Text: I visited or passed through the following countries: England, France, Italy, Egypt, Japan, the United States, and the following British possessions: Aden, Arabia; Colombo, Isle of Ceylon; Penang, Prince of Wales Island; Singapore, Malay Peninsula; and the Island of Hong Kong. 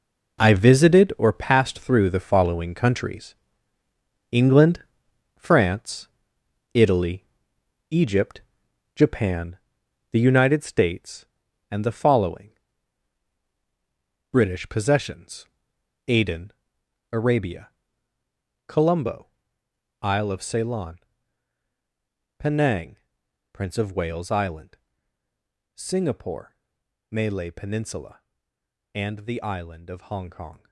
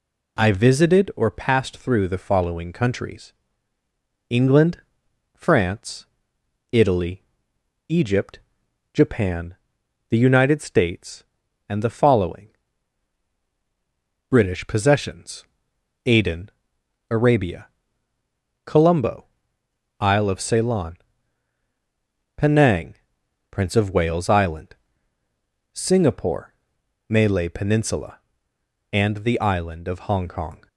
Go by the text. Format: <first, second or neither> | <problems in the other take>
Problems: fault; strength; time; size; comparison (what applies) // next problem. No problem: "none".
second | gets quieter; strong; throughout; 11.5 dB // pauses between "following" and "British"; strong; at 12.5 s; 1.8 s long; strong in the second